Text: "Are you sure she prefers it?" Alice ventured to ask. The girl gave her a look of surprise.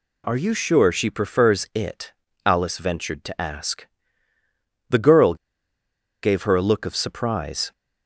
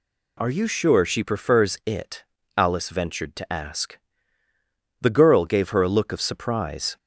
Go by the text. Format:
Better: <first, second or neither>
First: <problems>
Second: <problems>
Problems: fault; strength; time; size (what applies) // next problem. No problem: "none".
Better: second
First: pauses between "girl" and "gave"; noticeable; at 5.3 s; 0.87 s long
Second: none